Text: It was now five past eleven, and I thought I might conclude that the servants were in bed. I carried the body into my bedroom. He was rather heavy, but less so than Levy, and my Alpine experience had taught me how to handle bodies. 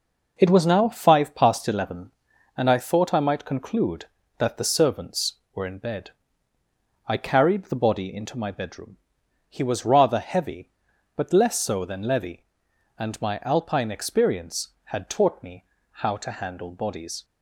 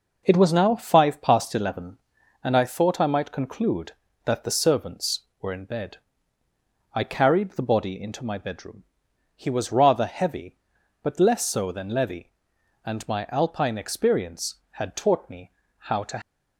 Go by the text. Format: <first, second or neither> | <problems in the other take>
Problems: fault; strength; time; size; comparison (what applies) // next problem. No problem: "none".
first | pauses between "me" and "how"; slight; at 15.5 s; 0.26 s long; slight in the first // stops before "handle bodies"; at 16.2 s